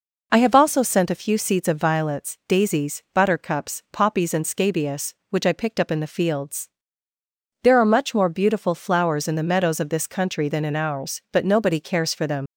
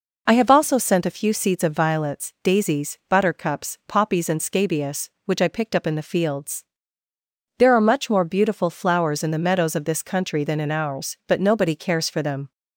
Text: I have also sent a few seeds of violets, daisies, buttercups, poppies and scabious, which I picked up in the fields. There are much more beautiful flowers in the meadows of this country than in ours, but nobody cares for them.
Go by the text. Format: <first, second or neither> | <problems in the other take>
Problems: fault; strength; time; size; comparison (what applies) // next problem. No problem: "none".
second | leaves "them" unfinished; at 12.4 s; 100 ms